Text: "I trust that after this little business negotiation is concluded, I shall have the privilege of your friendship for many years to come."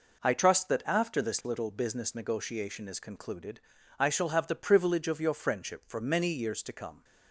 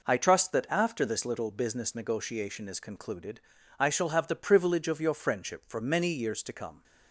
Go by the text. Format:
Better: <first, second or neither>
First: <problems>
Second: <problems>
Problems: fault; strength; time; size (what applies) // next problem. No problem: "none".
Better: neither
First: none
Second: none